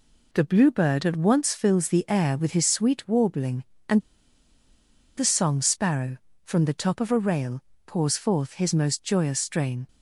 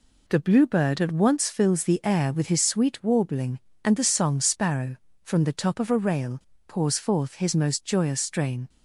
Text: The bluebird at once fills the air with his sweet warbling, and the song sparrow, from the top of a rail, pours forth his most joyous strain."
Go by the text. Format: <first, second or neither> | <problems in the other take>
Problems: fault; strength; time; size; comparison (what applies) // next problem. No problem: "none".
second | pauses between "and" and "the"; at 3.9 s; 1.1 s long